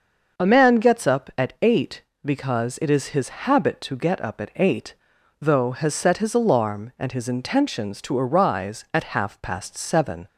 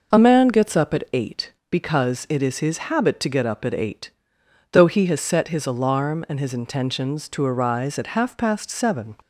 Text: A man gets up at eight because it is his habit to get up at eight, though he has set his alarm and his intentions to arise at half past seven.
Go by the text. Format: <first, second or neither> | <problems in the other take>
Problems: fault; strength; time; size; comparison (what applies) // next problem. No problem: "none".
second | starts louder than the rest; until 1.4 s; 6 dB // skips "he"; at 5.7 s